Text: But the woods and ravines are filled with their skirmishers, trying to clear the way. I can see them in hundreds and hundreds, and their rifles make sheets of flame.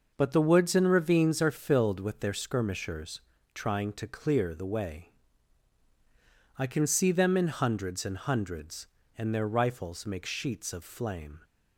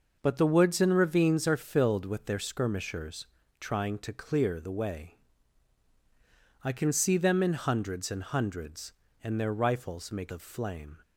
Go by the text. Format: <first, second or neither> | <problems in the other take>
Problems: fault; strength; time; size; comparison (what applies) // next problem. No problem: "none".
first | skips "sheets"; at 10.3 s